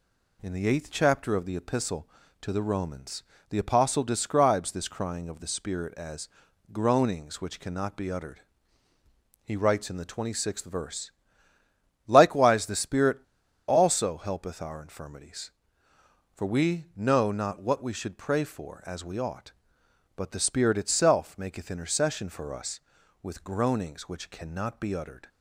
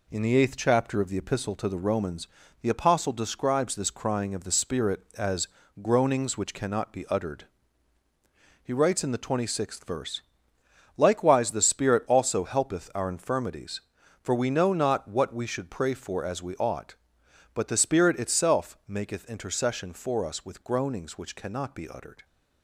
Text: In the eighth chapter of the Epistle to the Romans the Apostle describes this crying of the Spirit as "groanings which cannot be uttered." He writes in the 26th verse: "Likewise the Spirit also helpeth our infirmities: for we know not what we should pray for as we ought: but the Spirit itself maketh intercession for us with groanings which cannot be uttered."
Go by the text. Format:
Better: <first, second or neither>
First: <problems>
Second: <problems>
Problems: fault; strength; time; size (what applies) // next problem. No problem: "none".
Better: second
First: pauses between "Romans" and "the"; slight; at 3.2 s; 0.26 s long // pauses between "as" and "groanings"; at 6.2 s; 0.42 s long // pauses between "Spirit" and "also"; noticeable; at 13.1 s; 0.48 s long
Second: pauses between "Romans" and "the"; slight; at 2.2 s; 0.34 s long // pauses between "as" and "groanings"; slight; at 5.4 s; 0.34 s long